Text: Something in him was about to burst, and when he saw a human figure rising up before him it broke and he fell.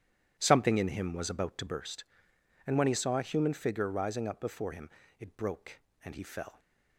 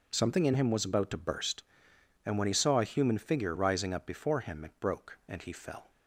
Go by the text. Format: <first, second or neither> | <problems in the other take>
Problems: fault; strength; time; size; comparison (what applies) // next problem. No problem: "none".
second | starts louder than the rest; strong; until 1.9 s; 11 dB // pauses between "him" and "it"; slight; at 4.8 s; 0.28 s long